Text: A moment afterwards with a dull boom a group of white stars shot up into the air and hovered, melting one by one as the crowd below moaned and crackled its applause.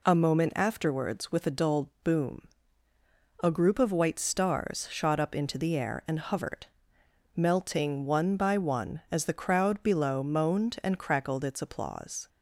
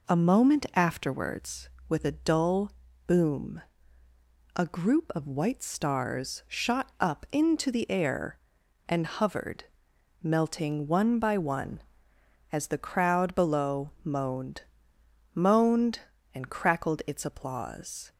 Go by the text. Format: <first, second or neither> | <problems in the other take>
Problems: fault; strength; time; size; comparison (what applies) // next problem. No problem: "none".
first | pauses between "dull" and "boom"; slight; at 2.7 s; 0.36 s long // pauses between "boom" and "a"; noticeable; at 3.6 s; 0.92 s long; noticeable in the first // says "moaned" twice; at 15.3 s